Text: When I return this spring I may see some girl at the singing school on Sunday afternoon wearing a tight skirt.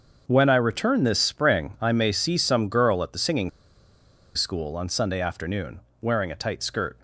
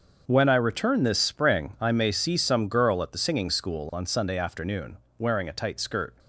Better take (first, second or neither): second